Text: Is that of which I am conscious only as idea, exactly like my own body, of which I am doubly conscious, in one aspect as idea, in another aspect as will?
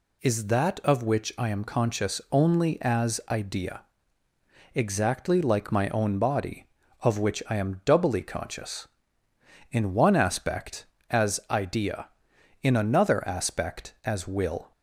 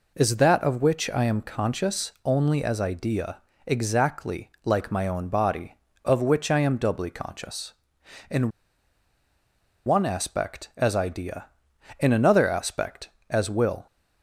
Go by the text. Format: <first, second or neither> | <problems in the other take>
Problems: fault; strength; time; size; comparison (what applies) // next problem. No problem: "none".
first | pauses between "in" and "one"; strong; at 8.4 s; 1.3 s long